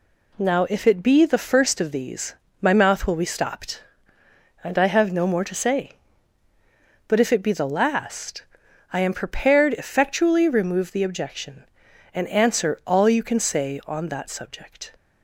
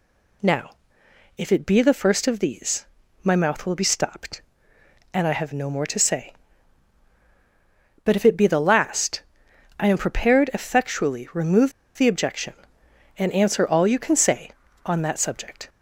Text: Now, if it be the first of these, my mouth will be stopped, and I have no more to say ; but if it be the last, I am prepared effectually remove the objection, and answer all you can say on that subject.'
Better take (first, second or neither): first